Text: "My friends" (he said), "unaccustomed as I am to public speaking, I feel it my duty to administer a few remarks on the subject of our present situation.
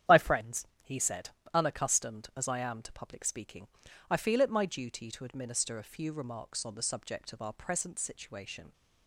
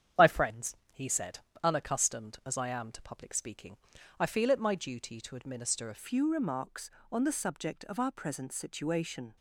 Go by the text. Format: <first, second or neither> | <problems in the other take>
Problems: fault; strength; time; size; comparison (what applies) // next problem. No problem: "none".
first | starts louder than the rest; strong; until 1.3 s; 8.5 dB; strong in the first // changes voice at "few"; from 5.9 s on; 3.4 s long